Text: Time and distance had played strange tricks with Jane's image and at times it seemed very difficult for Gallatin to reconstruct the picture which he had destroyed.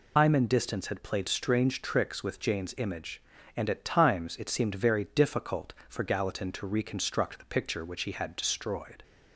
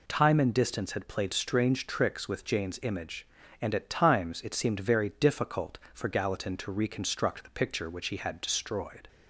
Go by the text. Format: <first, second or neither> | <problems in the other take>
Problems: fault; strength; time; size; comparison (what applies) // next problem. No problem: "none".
second | loses the start of "Time"; at 0.1 s; 135 ms